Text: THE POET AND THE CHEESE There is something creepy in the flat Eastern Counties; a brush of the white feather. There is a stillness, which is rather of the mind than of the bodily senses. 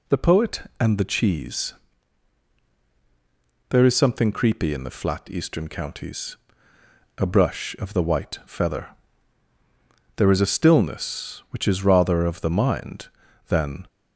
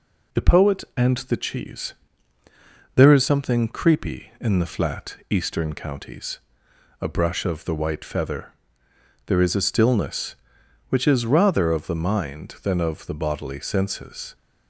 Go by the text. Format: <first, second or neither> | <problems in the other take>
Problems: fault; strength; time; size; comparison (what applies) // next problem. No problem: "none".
second | pauses between "CHEESE" and "There"; strong; at 1.7 s; 1.9 s long; also in the second // stops before "of the bodily senses"; at 13.8 s